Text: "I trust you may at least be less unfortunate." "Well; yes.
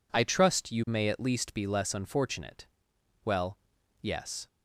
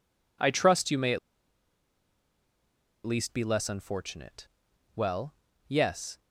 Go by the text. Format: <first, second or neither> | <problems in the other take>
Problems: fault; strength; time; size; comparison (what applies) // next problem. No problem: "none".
first | pauses between "at" and "least"; strong; at 1.1 s; 1.8 s long